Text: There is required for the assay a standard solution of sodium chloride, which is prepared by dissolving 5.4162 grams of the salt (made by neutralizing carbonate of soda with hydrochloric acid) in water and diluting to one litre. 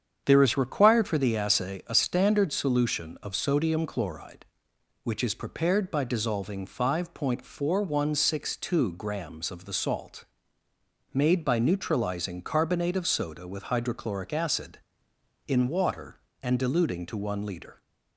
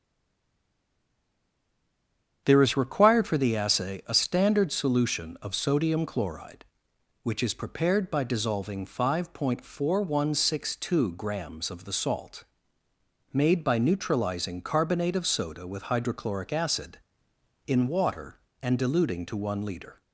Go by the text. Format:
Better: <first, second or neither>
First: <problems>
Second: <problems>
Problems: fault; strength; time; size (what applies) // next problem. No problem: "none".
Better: first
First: starts louder than the rest; strong; until 1.2 s; 8 dB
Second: stays silent before the first word; until 2.4 s; 2.4 s long // starts louder than the rest; strong; until 3.4 s; 8 dB